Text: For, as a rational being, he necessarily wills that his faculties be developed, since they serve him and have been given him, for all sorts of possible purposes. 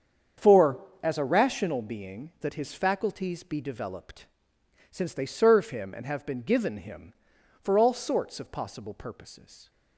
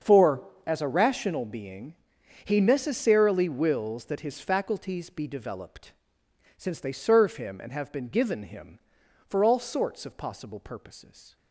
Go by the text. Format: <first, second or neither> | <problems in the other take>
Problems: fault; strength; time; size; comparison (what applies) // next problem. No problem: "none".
second | starts louder than the rest; strong; until 1.6 s; 7.5 dB; also in the second // skips "he necessarily wills"; at 2.3 s